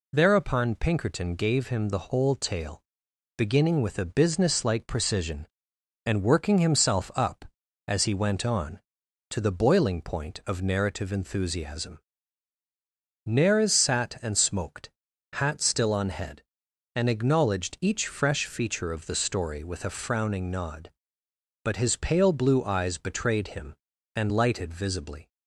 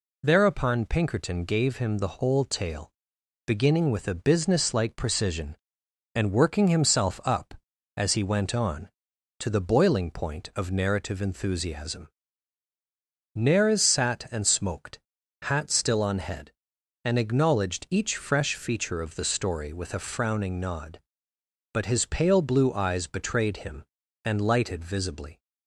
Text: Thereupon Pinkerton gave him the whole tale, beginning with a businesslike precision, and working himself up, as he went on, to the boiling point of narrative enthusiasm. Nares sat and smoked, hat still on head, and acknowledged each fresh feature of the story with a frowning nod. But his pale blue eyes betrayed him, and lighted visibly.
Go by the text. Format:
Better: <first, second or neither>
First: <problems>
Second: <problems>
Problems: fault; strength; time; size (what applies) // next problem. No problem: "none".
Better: neither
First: none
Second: none